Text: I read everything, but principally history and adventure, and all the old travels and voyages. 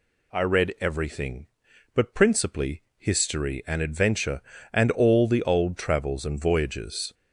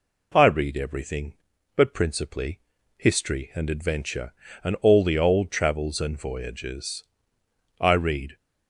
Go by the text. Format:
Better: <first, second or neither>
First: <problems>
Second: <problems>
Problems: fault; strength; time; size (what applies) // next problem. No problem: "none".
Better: first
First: pauses between "principally" and "history"; slight; at 2.8 s; 0.16 s long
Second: pauses between "principally" and "history"; at 2.5 s; 0.38 s long // goes on to say "I read"; from 7.8 s on; 0.56 s long